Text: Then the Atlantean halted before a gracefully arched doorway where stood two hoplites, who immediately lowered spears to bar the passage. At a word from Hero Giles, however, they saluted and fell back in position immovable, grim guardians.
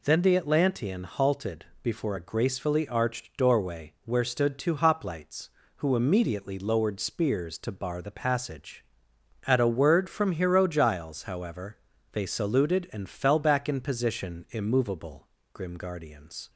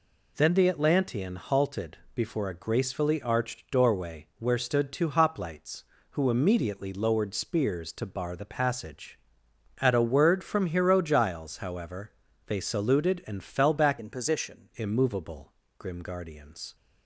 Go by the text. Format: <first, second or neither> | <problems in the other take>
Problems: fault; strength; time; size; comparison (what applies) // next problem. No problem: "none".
first | pauses between "halted" and "before"; slight; at 1.9 s; 0.16 s long; slight in the first // changes voice from "in" to "position"; from 13.9 to 14.6 s; 0.7 s long